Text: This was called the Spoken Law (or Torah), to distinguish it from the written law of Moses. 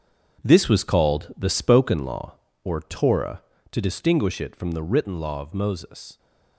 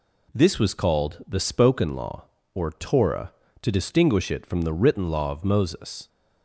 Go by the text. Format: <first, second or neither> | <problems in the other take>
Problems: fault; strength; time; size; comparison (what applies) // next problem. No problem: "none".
second | gets quieter; strong; throughout; 9.5 dB